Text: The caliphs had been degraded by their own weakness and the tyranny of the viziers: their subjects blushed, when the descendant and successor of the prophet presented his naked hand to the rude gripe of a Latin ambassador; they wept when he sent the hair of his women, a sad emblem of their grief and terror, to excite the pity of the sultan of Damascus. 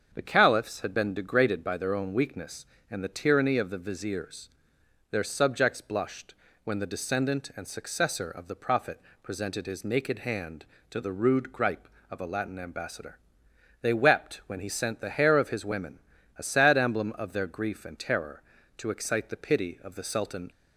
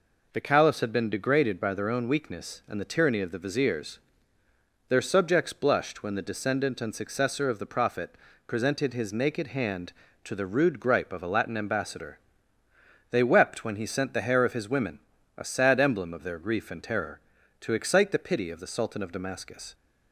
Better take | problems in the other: second | starts louder than the rest; strong; until 1.1 s; 7 dB // pauses between "prophet" and "presented"; slight; at 9.0 s; 0.22 s long; slight in the second // stops before "of Damascus"; at 20.5 s

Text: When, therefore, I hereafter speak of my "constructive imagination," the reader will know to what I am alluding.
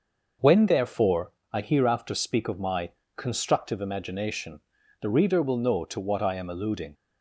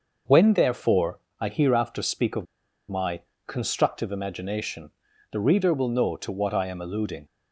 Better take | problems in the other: first | starts louder than the rest; noticeable; until 1.4 s; 6 dB; noticeable in the first // pauses between "of" and "my"; at 2.4 s; 0.45 s long // pauses between "my" and "constructive"; slight; at 3.2 s; 0.26 s long; slight in the first

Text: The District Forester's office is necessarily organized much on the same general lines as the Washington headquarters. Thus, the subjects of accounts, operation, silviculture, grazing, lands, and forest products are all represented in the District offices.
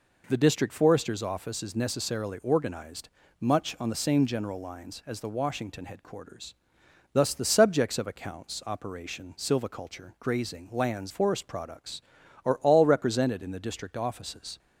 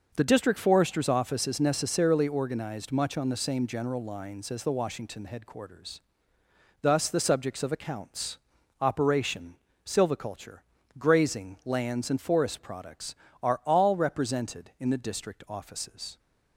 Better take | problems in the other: second | pauses between "organized" and "much"; slight; at 3.0 s; 0.30 s long // skips "and"; at 11.1 s

